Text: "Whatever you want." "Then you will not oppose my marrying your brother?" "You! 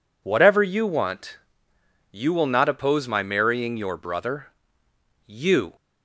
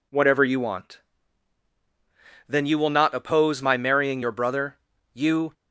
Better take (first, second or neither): second